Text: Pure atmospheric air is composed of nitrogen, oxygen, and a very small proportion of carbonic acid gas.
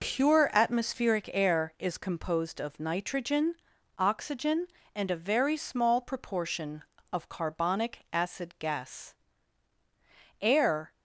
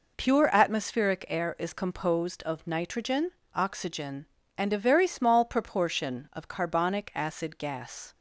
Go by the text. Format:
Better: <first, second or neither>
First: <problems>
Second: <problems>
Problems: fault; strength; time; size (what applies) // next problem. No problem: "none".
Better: second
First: goes on to say "Air"; from 10.4 s on; 0.52 s long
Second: none